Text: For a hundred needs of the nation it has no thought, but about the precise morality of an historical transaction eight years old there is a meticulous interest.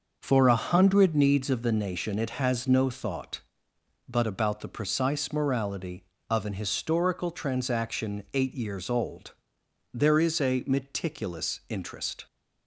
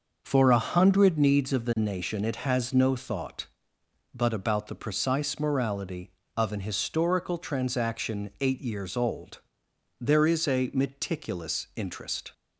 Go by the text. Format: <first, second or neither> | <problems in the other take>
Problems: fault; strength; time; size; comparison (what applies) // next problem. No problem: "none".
neither | pauses between "old" and "there"; noticeable; the same in both